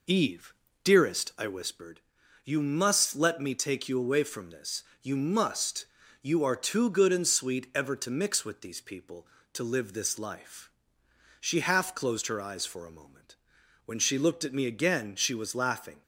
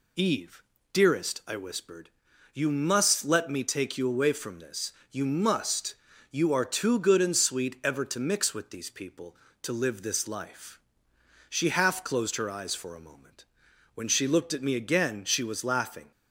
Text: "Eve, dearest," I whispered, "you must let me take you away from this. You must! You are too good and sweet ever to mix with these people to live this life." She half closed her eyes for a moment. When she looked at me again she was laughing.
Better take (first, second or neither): second